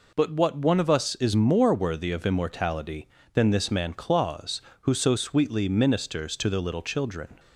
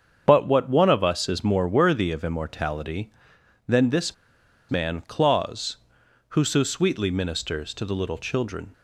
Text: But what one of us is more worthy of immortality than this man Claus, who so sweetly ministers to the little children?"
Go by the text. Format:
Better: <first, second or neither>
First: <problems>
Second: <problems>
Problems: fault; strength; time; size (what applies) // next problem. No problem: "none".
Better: first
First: none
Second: starts louder than the rest; strong; until 1.2 s; 7.5 dB // pauses between "this" and "man"; noticeable; at 4.1 s; 0.55 s long